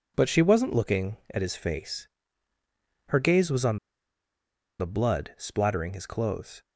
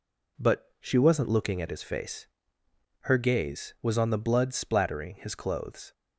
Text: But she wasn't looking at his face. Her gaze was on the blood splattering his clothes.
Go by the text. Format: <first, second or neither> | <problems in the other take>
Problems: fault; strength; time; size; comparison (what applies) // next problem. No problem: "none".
second | pauses between "on" and "the"; at 3.7 s; 1.0 s long